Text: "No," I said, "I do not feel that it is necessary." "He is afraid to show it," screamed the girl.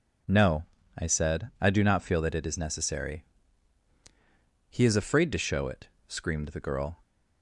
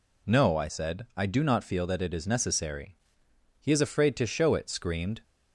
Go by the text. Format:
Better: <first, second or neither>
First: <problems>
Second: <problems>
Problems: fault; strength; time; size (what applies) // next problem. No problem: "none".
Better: first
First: none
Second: stops before "the girl"; at 5.2 s